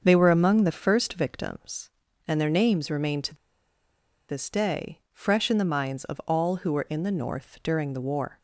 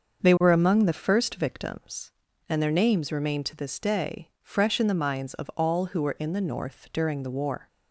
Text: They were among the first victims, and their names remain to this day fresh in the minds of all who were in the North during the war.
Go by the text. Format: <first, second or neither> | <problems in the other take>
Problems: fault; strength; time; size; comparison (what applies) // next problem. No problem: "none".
second | starts louder than the rest; until 1.0 s; 6.5 dB; also in the second // pauses between "to" and "this"; noticeable; at 3.3 s; 0.94 s long